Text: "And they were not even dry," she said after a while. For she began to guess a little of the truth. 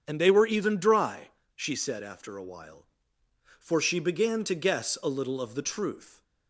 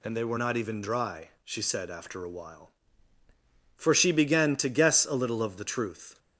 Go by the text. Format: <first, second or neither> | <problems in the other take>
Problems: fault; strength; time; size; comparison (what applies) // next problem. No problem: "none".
second | starts louder than the rest; strong; until 1.0 s; 7.5 dB // skips "not"; at 0.4 s